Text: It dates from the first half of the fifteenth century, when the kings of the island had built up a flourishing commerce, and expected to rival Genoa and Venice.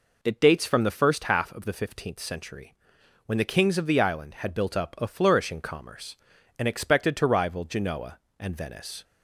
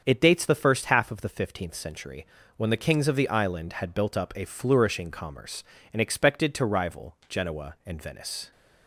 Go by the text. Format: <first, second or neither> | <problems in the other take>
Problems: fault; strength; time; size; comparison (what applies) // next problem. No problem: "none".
first | starts louder than the rest; until 1.0 s; 7 dB // skips "from"; at 0.4 s